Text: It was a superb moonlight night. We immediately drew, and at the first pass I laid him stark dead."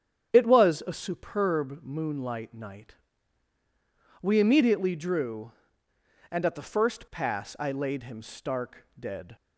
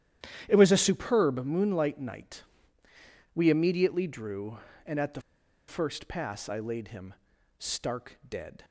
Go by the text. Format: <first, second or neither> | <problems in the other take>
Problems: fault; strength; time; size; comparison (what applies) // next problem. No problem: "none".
first | starts louder than the rest; strong; until 1.4 s; 11 dB; strong in the first // pauses between "the" and "first"; noticeable; at 5.1 s; 0.48 s long // pauses between "him" and "stark"; at 7.1 s; 0.44 s long